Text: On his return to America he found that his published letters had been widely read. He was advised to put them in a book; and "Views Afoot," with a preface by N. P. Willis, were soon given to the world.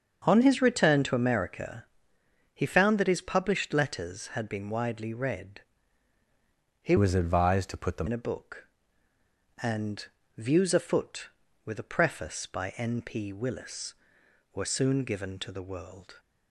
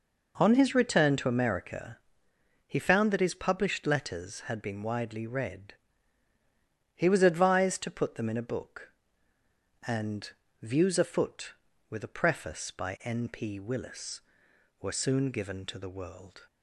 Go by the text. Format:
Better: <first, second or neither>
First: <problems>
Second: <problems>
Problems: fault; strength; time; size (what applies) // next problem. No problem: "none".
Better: second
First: starts louder than the rest; until 1.2 s; 7 dB // pauses between "America" and "he"; noticeable; at 1.8 s; 0.70 s long // changes voice from "was" to "them"; from 6.9 to 8.0 s; 1.1 s long // pauses between "and" and "Views"; slight; at 10.0 s; 0.30 s long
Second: pauses between "America" and "he"; noticeable; at 1.9 s; 0.70 s long // pauses between "and" and "Views"; slight; at 10.3 s; 0.30 s long